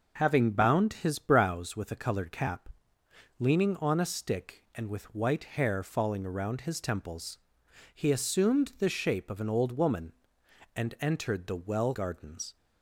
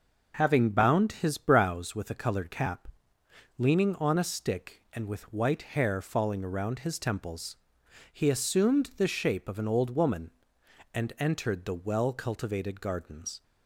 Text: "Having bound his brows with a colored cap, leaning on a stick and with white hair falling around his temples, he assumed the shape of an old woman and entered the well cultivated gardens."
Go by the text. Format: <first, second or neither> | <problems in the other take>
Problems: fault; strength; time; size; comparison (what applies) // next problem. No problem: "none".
second | skips "cultivated"; at 11.9 s